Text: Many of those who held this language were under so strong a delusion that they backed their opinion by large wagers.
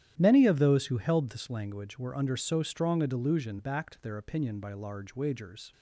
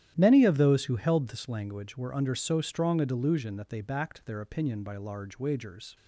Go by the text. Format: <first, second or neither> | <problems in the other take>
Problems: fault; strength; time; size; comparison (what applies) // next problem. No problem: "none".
second | starts louder than the rest; strong; until 1.1 s; 11.5 dB; strong in the second // skips "that they"; at 3.5 s